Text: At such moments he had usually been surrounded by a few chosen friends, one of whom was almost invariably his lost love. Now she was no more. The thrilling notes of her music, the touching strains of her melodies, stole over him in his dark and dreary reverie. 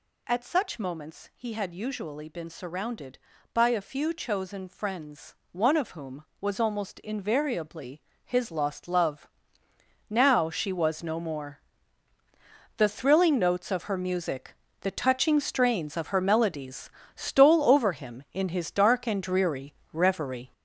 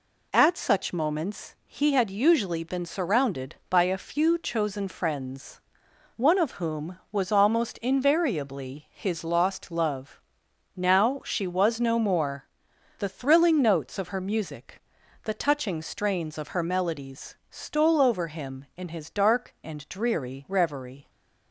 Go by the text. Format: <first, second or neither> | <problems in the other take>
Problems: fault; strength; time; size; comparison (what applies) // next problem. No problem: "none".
second | gets louder; throughout; 6.5 dB // pauses between "invariably" and "his"; slight; at 8.0 s; 0.24 s long // pauses between "dreary" and "reverie"; slight; at 19.7 s; 0.18 s long